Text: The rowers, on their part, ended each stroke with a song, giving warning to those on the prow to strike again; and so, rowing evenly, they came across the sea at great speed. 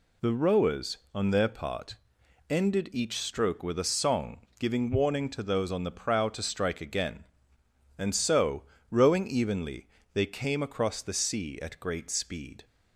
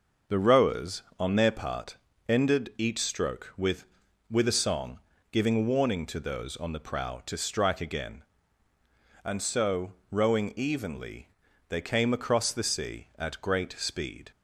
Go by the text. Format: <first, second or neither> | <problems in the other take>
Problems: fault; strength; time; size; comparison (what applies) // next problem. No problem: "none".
first | says "with" twice; at 4.3 s